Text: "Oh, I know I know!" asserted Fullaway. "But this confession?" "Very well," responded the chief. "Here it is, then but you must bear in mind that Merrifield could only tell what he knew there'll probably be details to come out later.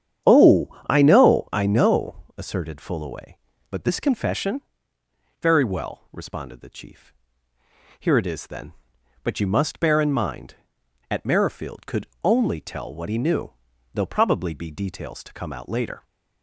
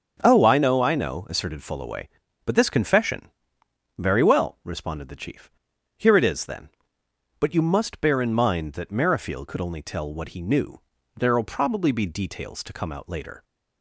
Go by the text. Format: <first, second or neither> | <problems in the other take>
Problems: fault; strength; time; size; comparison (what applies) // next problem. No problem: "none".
second | starts louder than the rest; strong; until 1.4 s; 9 dB; also in the second // says "at" for "that"; at 11.1 s // pauses between "could" and "only"; slight; at 12.0 s; 0.16 s long // pauses between "knew" and "there'll"; at 13.5 s; 0.42 s long; slight in the second